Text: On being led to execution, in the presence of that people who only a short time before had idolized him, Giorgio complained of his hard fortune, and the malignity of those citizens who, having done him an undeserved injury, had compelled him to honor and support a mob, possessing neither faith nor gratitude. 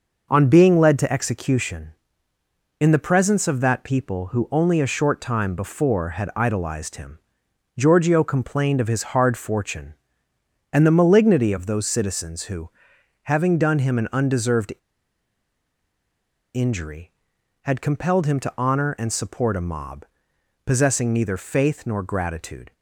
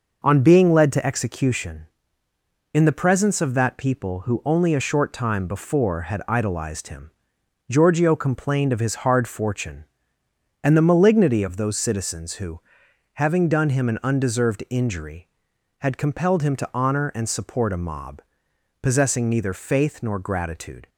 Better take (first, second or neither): second